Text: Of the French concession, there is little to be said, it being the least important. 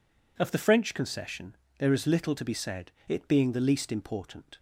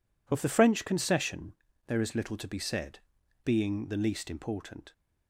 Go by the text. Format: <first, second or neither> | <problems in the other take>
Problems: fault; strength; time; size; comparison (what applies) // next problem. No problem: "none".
first | skips "it"; at 3.2 s